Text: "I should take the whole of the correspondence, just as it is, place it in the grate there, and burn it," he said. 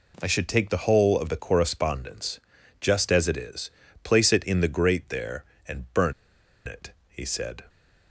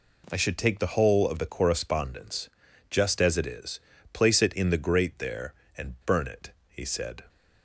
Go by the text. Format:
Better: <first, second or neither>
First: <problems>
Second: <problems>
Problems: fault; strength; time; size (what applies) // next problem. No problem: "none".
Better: second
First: pauses between "burn" and "it"; noticeable; at 6.1 s; 0.54 s long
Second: none